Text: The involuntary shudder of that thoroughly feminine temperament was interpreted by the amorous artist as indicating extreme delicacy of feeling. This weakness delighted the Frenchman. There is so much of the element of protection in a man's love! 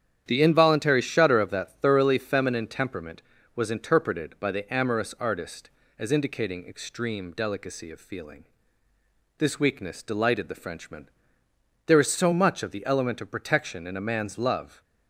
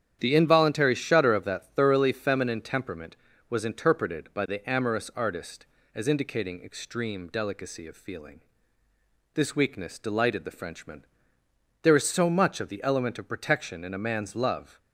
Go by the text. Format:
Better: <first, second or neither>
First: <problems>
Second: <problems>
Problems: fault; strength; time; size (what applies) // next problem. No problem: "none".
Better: neither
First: starts louder than the rest; strong; until 1.2 s; 9.5 dB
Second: starts louder than the rest; strong; until 1.2 s; 9.5 dB